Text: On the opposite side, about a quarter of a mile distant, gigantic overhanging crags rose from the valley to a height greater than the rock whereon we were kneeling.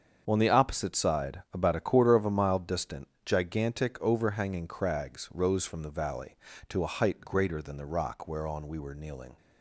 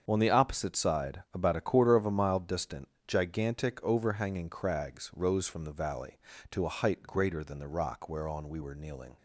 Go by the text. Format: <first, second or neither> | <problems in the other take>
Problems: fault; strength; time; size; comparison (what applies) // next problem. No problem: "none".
neither | starts louder than the rest; the same in both